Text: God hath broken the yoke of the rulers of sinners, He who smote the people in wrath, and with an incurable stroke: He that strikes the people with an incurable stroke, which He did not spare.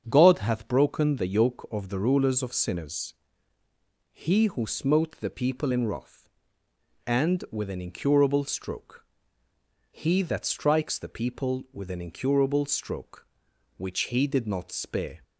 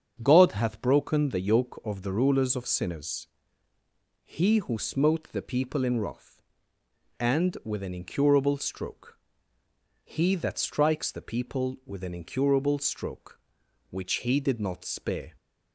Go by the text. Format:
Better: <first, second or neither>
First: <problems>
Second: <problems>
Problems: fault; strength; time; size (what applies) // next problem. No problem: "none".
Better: neither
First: starts louder than the rest; strong; until 1.0 s; 7 dB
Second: starts louder than the rest; strong; until 1.2 s; 7 dB